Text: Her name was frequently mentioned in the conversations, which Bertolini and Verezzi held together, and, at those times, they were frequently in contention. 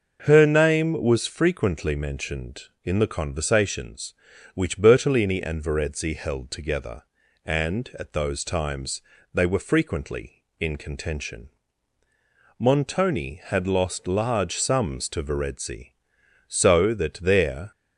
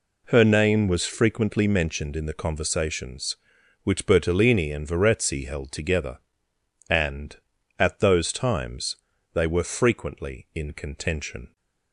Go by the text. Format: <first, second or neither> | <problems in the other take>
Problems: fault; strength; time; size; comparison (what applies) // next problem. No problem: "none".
second | starts louder than the rest; until 1.2 s; 6.5 dB // goes on to say "Montoni had lost large sums to Verezzi so that there"; strong; from 12.5 s on; 5.1 s long